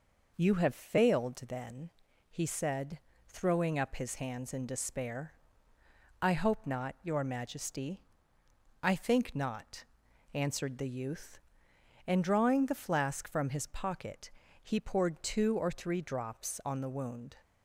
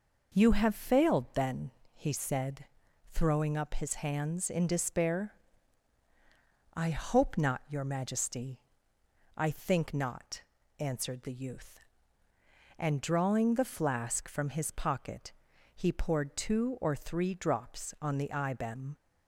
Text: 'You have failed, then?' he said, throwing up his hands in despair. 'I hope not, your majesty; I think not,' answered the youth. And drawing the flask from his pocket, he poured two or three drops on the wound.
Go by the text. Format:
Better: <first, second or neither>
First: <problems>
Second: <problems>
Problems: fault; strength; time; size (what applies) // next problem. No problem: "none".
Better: first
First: none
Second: says "ibem" for "wound"; at 18.3 s